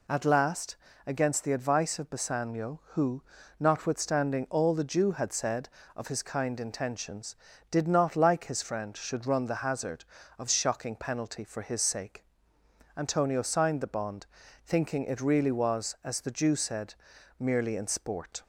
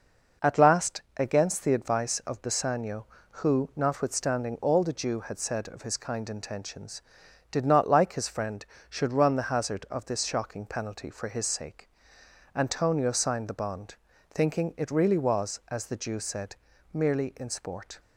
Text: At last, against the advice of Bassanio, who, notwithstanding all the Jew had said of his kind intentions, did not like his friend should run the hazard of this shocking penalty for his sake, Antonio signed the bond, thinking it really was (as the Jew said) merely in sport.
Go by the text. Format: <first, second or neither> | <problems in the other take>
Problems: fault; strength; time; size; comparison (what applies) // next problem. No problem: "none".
second | skips "this"; at 10.4 s